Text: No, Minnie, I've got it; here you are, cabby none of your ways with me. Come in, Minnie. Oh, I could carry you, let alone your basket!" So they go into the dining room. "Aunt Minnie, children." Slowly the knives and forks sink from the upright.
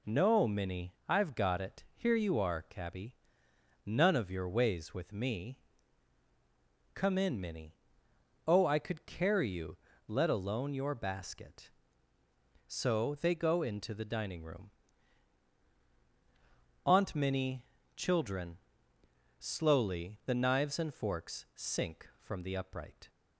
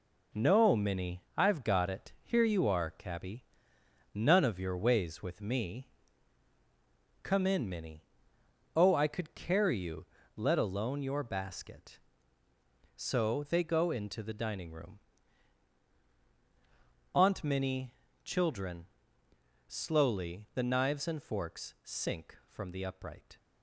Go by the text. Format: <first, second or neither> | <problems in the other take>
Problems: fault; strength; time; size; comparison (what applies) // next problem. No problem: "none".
first | gets quieter; strong; throughout; 7 dB // pauses between "cabby" and "none"; noticeable; at 3.4 s; 0.68 s long; noticeable in the first